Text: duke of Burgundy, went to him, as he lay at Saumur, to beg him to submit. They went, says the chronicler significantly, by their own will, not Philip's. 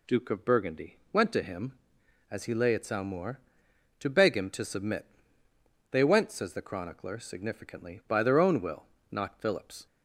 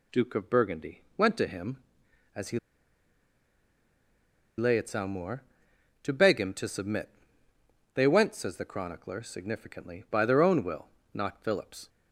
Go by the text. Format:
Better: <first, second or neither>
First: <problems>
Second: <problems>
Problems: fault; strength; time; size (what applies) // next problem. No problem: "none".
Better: first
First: none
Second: pauses between "he" and "lay"; strong; at 2.5 s; 2.0 s long